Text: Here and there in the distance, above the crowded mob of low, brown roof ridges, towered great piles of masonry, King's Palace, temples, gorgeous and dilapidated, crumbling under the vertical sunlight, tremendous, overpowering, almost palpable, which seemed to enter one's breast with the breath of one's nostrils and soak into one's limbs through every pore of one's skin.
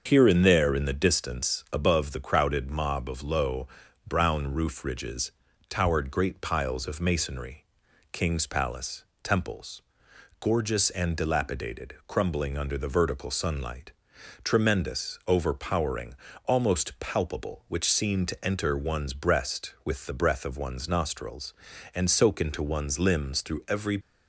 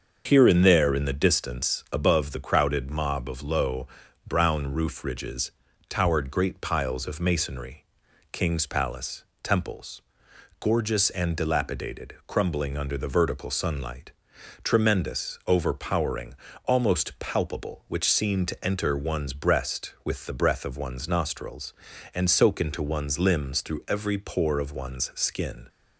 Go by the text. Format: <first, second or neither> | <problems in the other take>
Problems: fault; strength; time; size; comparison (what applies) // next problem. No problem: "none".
second | starts louder than the rest; until 1.0 s; 6.5 dB; also in the second // stops before "pore of one's skin"; at 24.0 s